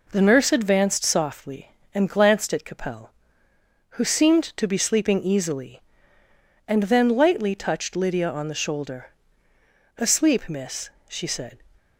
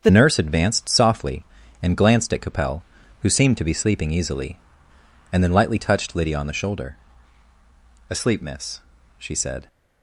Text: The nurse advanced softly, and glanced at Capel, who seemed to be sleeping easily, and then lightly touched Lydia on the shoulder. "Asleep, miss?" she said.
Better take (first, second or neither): first